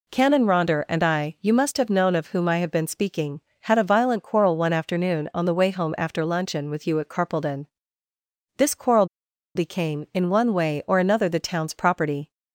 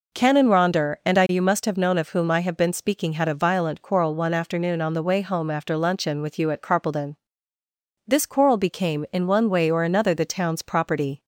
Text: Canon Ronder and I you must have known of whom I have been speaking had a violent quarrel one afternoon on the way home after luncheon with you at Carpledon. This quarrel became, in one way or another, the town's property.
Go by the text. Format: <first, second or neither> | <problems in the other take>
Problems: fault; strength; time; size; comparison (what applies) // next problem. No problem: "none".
second | pauses between "quarrel" and "became"; noticeable; at 9.0 s; 0.50 s long